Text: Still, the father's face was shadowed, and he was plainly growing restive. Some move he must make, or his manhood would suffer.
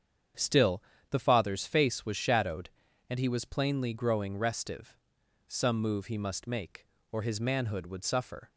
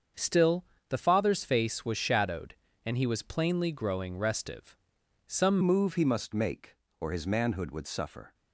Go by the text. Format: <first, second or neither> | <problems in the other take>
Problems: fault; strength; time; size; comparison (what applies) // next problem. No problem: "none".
first | starts louder than the rest; until 1.4 s; 7 dB; strong in the first // changes voice at "move"; from 5.6 s on; 2.7 s long